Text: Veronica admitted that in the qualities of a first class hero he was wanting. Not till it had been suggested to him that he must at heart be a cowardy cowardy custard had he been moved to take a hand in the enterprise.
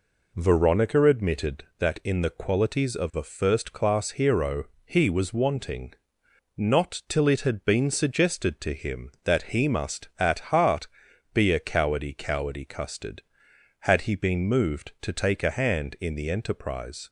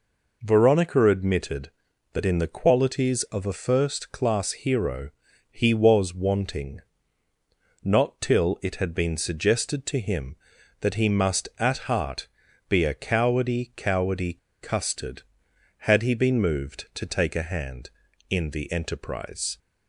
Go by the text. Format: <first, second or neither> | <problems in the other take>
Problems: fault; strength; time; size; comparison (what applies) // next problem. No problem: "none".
first | pauses between "hero" and "he"; at 5.1 s; 0.40 s long; slight in the first // pauses between "heart" and "be"; at 12.2 s; 0.40 s long; noticeable in the first // pauses between "cowardy" and "custard"; slight; at 14.3 s; 0.23 s long